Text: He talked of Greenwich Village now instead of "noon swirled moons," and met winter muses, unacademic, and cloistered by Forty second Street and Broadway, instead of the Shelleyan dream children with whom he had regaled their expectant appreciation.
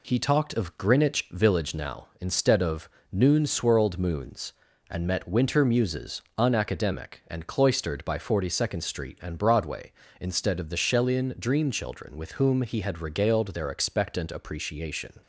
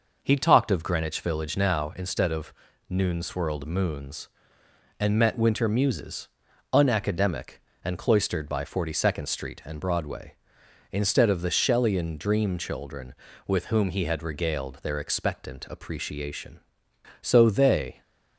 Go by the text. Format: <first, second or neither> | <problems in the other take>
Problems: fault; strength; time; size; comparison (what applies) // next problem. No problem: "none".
first | pauses between "of" and "noon"; at 2.5 s; 0.38 s long; slight in the first // goes on to say "So they"; noticeable; from 17.2 s on; 0.80 s long